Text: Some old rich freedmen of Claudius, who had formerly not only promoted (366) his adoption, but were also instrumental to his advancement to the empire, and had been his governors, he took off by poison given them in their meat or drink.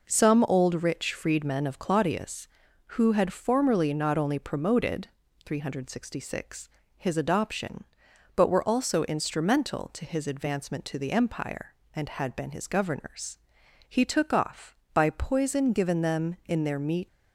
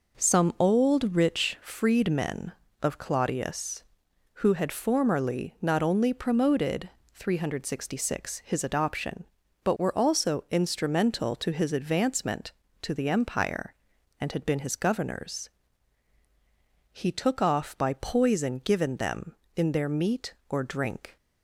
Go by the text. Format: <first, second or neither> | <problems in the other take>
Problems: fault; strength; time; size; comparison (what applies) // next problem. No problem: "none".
second | stops before "or drink"; at 17.0 s